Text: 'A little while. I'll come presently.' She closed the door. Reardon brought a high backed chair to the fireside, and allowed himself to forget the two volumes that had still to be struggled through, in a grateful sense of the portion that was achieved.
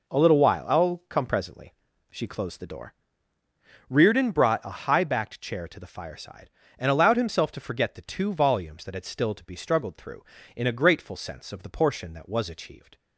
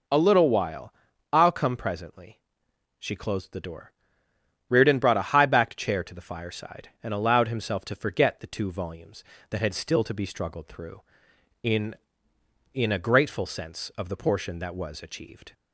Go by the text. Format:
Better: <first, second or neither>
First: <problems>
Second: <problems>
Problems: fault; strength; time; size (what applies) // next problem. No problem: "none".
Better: first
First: none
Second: says "in" twice; at 12.7 s